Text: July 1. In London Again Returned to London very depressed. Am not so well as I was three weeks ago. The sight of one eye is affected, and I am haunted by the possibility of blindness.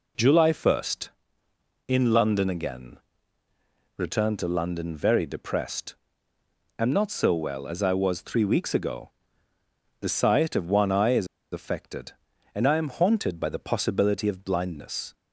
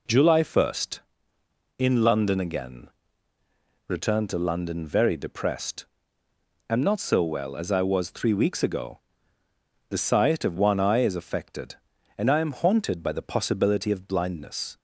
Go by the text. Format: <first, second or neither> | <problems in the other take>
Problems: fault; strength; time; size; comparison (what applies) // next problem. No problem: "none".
second | pauses between "Again" and "Returned"; at 2.9 s; 1.0 s long; also in the second // pauses between "is" and "affected"; slight; at 11.2 s; 0.26 s long